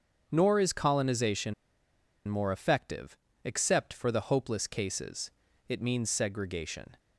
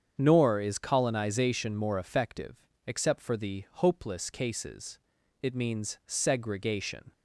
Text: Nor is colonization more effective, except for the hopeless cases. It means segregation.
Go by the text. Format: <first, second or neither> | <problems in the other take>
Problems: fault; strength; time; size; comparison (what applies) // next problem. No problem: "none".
second | starts louder than the rest; strong; until 1.3 s; 7.5 dB; strong in the second // pauses between "colonization" and "more"; noticeable; at 1.5 s; 0.74 s long